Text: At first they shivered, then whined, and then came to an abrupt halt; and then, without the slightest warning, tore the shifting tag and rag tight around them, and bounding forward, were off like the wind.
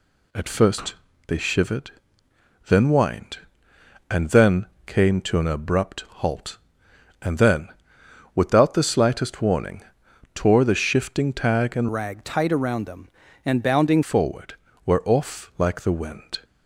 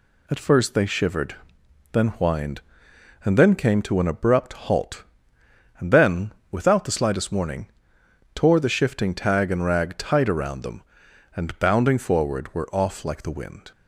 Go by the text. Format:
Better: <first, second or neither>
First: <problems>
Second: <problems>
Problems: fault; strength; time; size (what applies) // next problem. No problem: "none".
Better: second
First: pauses between "first" and "they"; slight; at 0.9 s; 0.32 s long // pauses between "then" and "came"; slight; at 4.6 s; 0.20 s long // changes voice from "rag" to "bounding"; from 11.9 to 14.0 s; 2.1 s long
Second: none